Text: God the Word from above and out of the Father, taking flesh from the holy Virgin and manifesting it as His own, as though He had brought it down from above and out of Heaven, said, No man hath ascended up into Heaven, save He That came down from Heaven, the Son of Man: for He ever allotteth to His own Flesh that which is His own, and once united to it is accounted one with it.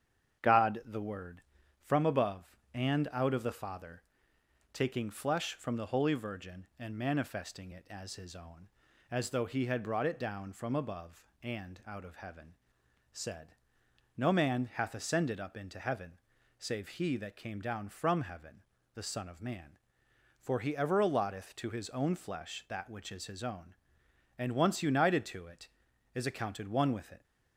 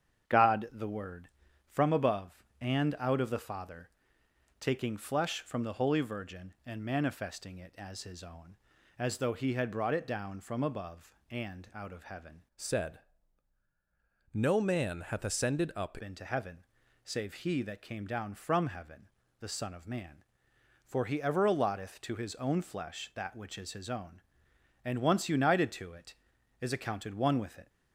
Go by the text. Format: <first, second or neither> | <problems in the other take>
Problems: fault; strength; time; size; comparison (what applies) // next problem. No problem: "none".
first | starts louder than the rest; strong; until 1.7 s; 8.5 dB; strong in the first // changes voice from "said" to "up"; from 12.5 to 15.9 s; 3.4 s long